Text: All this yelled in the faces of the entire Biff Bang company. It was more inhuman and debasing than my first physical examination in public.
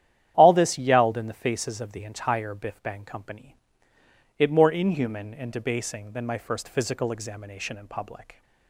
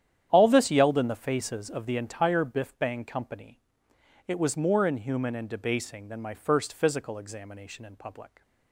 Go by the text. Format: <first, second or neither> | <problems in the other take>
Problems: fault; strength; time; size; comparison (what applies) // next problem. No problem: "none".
second | starts louder than the rest; strong; until 1.3 s; 10.5 dB; strong in the second // skips "was"; at 4.4 s